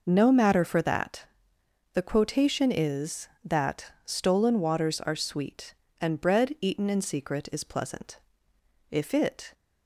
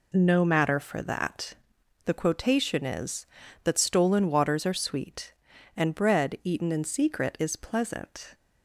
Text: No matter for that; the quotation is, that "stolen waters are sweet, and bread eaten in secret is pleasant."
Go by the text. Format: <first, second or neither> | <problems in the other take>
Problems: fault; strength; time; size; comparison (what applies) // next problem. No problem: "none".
second | goes on to say "If it"; noticeable; from 8.9 s on; 0.62 s long